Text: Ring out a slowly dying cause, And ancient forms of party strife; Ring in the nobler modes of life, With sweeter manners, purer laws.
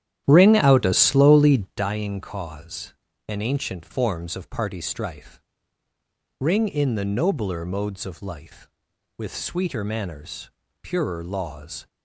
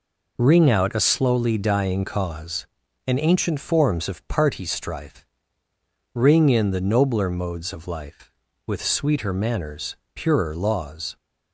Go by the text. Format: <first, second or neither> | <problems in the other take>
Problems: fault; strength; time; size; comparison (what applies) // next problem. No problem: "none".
second | starts louder than the rest; strong; until 1.9 s; 11 dB